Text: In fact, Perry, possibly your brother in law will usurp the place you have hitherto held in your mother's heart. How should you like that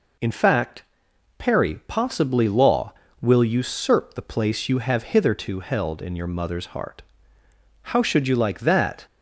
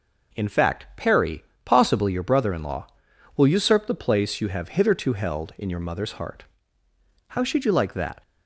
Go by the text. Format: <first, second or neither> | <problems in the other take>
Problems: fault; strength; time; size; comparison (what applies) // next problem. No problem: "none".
second | skips "your brother in"; at 2.4 s